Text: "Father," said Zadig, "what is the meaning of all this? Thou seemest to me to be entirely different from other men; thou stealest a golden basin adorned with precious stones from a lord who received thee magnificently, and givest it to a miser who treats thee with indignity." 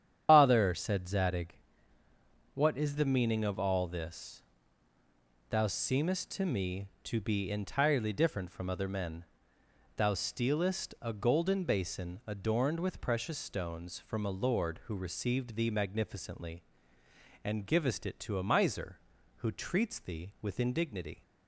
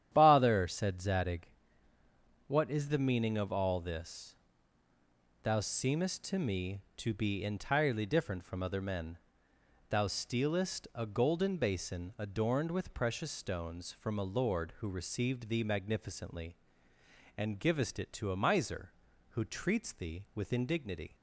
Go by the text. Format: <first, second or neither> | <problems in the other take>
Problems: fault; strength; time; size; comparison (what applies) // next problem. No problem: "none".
second | loses the start of "Father"; at 0.2 s; 100 ms // starts louder than the rest; strong; until 1.3 s; 9 dB; strong in the second